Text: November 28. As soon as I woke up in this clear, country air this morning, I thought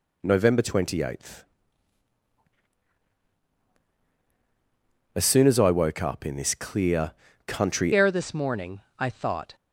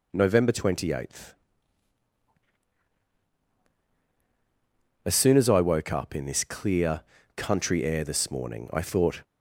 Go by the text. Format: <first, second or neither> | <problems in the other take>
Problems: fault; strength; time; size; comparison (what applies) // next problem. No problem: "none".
second | changes voice at "air"; from 7.9 s on; 1.6 s long